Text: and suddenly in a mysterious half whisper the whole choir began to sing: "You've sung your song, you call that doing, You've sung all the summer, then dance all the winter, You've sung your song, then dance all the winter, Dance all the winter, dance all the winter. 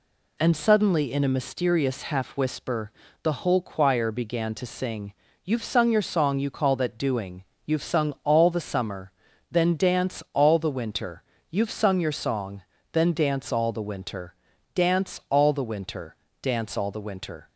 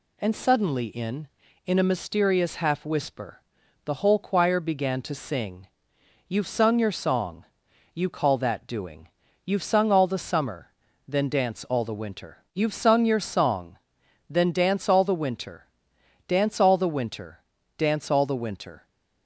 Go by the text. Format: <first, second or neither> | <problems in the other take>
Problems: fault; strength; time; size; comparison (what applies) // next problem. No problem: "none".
first | says "in" twice; at 1.6 s // pauses between "whisper" and "the"; at 3.4 s; 0.44 s long; slight in the first